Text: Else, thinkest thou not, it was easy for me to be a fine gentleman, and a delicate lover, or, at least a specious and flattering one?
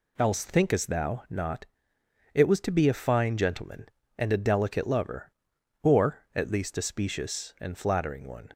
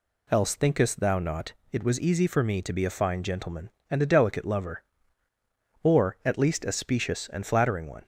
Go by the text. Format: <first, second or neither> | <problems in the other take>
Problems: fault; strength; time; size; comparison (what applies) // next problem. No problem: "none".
second | skips "easy for me"; at 2.6 s